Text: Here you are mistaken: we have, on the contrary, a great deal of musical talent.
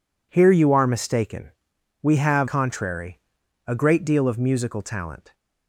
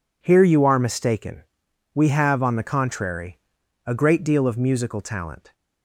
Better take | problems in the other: second | skips "on the"; at 2.4 s

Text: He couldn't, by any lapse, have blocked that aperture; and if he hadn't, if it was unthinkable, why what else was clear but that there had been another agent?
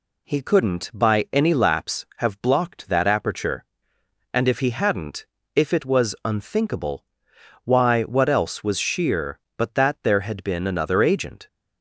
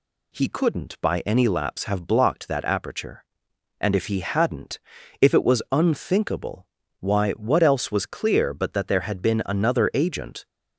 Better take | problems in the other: second | says "sheer" for "clear"; at 8.7 s

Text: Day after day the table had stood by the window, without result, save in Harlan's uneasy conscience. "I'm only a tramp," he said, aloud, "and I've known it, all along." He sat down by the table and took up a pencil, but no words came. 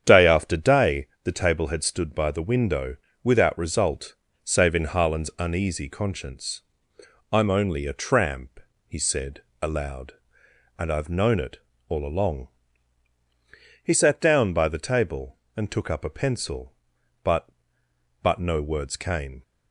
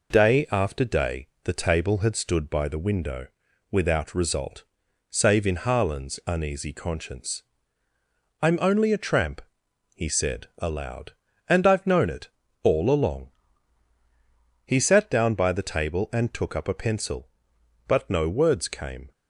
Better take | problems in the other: second | starts louder than the rest; strong; until 1.0 s; 9 dB // pauses between "day" and "the"; slight; at 1.0 s; 0.18 s long; slight in the second // says "but" twice; at 18.2 s

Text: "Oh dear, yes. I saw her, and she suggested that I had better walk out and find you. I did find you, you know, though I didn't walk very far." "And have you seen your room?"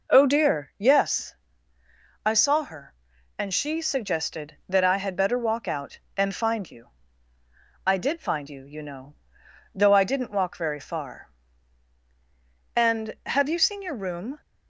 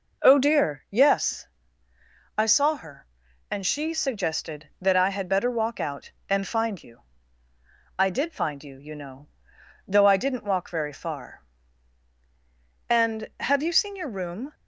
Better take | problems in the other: neither | none

